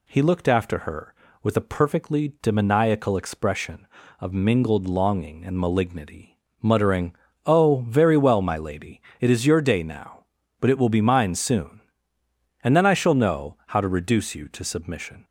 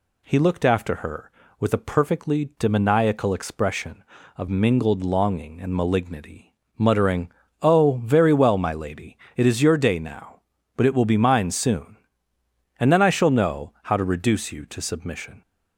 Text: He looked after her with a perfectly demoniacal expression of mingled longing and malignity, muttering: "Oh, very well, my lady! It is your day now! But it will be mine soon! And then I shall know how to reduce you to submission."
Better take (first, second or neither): neither